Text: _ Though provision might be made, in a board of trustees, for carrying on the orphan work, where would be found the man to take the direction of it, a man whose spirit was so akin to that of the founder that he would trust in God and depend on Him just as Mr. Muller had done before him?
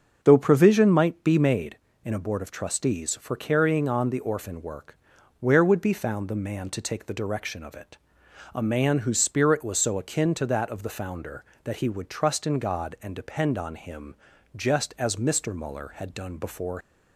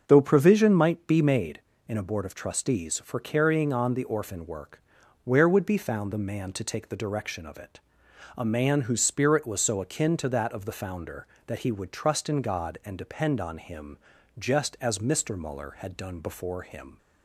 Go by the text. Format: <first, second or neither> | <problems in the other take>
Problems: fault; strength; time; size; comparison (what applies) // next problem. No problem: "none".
second | starts louder than the rest; until 1.2 s; 6.5 dB; also in the second // pauses between "Him" and "just"; at 14.1 s; 0.40 s long; also in the second // stops before "him"; at 16.8 s